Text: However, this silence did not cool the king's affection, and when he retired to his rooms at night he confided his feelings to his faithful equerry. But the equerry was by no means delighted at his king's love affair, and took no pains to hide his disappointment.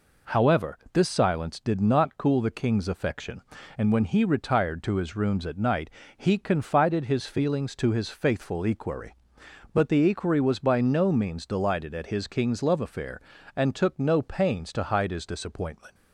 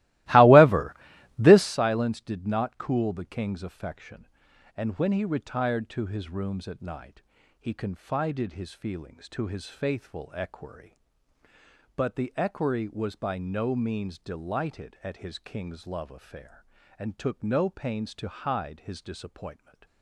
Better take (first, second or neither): first